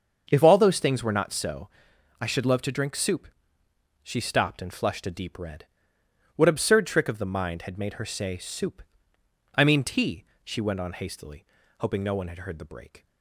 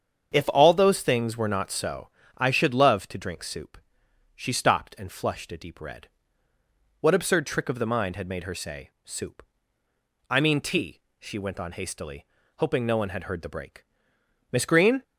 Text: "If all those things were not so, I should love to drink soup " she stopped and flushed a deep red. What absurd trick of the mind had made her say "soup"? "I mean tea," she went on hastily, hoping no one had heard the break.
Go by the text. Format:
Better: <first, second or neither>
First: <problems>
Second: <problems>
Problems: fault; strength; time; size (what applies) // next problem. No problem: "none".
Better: first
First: starts louder than the rest; until 1.3 s; 6.5 dB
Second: starts louder than the rest; strong; until 1.3 s; 7.5 dB // pauses between "say" and "soup"; slight; at 8.8 s; 0.16 s long // goes on to say "Miss Green"; from 14.5 s on; 0.52 s long